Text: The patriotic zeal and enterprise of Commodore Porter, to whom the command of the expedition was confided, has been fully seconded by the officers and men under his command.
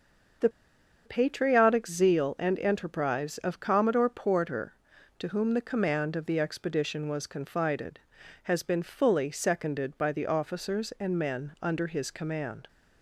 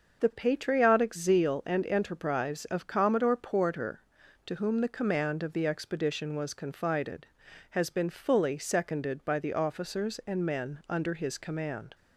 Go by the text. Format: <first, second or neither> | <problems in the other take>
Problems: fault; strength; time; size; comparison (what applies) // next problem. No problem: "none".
second | starts louder than the rest; until 1.9 s; 6.5 dB; also in the second // pauses between "The" and "patriotic"; noticeable; at 0.4 s; 0.55 s long